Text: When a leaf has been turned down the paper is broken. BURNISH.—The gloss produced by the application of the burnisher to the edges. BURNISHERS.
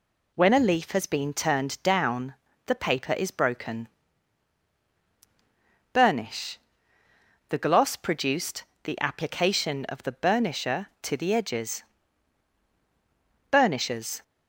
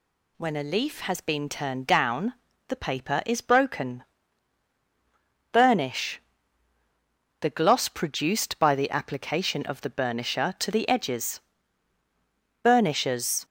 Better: second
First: pauses between "down" and "the"; slight; at 2.3 s; 0.30 s long // skips "by"; at 8.7 s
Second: pauses between "down" and "the"; slight; at 2.3 s; 0.32 s long

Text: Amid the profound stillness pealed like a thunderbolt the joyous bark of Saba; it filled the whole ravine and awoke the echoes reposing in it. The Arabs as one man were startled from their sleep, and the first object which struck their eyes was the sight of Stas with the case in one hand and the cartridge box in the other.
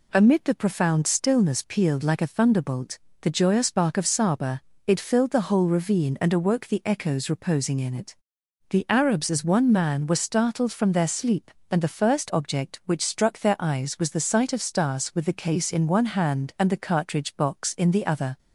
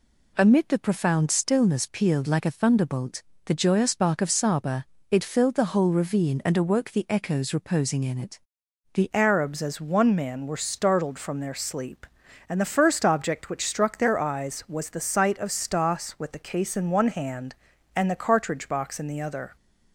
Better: first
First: pauses between "thunderbolt" and "the"; slight; at 2.9 s; 0.24 s long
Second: pauses between "thunderbolt" and "the"; slight; at 3.2 s; 0.24 s long // changes voice at "Arabs"; from 9.1 s on; 10.4 s long

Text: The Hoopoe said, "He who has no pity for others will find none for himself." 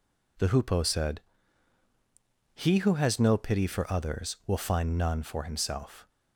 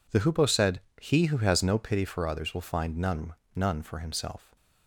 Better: first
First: none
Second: says "none" twice; at 3.5 s

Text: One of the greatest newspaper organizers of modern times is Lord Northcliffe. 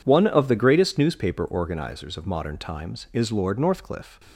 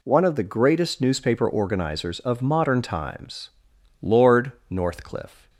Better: first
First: none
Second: skips "is"; at 3.7 s // pauses between "Lord" and "Northcliffe"; slight; at 4.5 s; 0.18 s long

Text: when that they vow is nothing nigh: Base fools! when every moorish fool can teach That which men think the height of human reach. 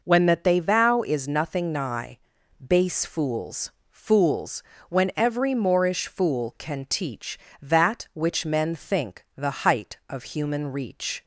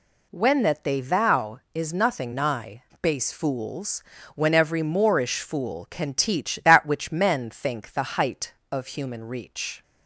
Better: second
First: says "fools" twice; at 3.9 s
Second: none

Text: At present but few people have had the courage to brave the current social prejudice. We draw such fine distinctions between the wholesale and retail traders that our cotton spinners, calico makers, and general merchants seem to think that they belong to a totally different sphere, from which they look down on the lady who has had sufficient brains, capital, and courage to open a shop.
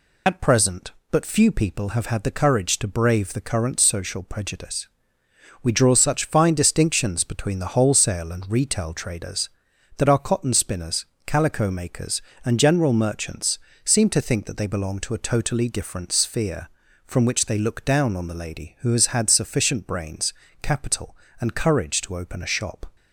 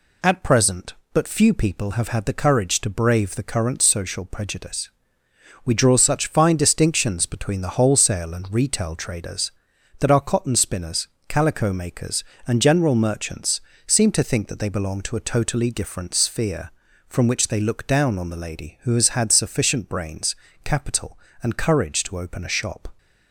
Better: second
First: loses the start of "At"; at 0.2 s; 45 ms // pauses between "merchants" and "seem"; slight; at 13.5 s; 0.24 s long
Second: pauses between "merchants" and "seem"; slight; at 13.6 s; 0.24 s long

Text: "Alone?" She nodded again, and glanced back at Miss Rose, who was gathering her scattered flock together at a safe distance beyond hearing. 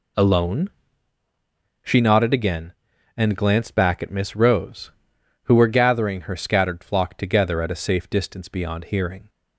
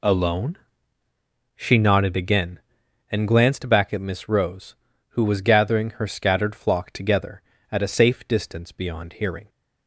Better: second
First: says "were" for "was"; at 5.5 s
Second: none

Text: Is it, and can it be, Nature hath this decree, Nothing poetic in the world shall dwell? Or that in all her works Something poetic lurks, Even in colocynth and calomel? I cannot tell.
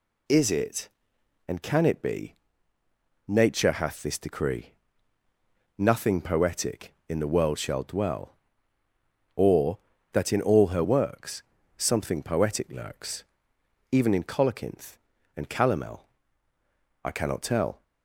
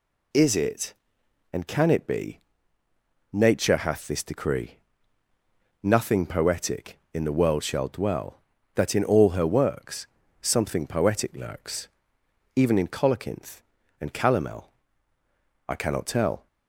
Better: first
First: pauses between "works" and "Something"; slight; at 11.4 s; 0.34 s long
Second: skips "Or"; at 8.5 s // pauses between "works" and "Something"; slight; at 10.0 s; 0.34 s long

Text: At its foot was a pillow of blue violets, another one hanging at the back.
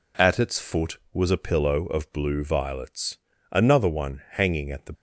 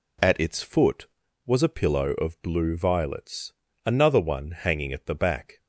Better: second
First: stops before "back"; at 4.9 s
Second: none

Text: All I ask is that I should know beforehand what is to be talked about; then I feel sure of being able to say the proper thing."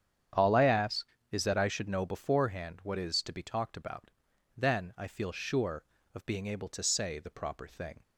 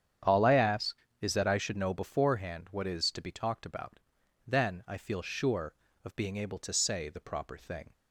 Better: neither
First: starts louder than the rest; strong; until 1.6 s; 9 dB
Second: starts louder than the rest; strong; until 1.5 s; 9 dB

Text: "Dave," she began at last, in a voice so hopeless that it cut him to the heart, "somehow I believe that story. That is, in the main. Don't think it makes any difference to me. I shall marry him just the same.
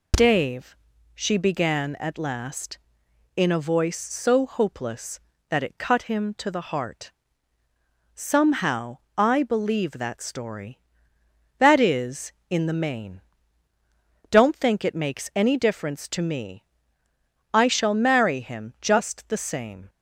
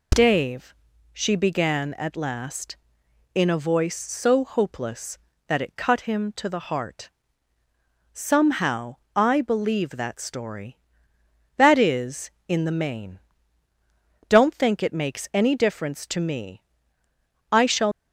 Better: first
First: pauses between "somehow" and "I"; slight; at 8.9 s; 0.18 s long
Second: pauses between "somehow" and "I"; slight; at 8.9 s; 0.18 s long // stops before "marry him just the same"; at 17.9 s

